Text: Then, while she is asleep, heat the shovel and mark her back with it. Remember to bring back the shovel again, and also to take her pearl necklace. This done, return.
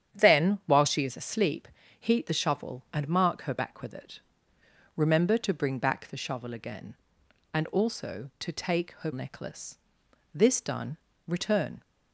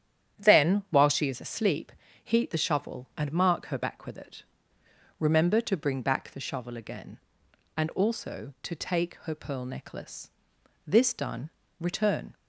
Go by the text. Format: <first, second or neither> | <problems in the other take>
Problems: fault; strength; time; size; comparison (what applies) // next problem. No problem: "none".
second | starts louder than the rest; strong; until 1.2 s; 9 dB; strong in the second // skips "pearl"; at 9.1 s